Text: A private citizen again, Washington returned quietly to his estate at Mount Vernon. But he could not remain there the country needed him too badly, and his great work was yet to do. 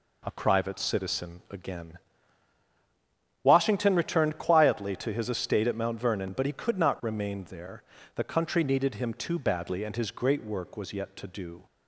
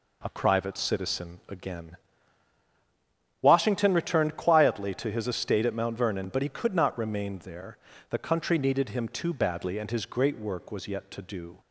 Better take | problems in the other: neither | pauses between "there" and "the"; slight; the same in both

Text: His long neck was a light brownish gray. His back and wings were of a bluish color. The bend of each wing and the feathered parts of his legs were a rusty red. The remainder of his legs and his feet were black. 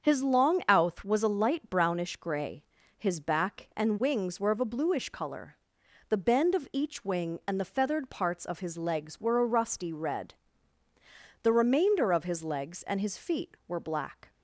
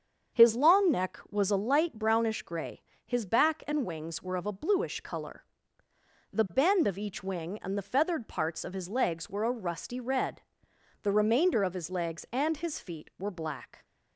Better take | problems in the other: second | starts louder than the rest; until 1.0 s; 7 dB; also in the second // says "outh" for "neck"; at 0.6 s

